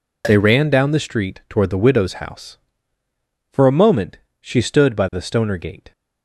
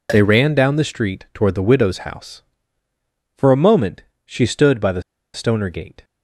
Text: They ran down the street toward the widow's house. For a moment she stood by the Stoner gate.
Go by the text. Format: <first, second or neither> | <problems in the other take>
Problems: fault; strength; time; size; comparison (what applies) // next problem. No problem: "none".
first | pauses between "moment" and "she"; slight; at 4.0 s; 0.22 s long; slight in the first // pauses between "the" and "Stoner"; slight; at 5.0 s; 0.31 s long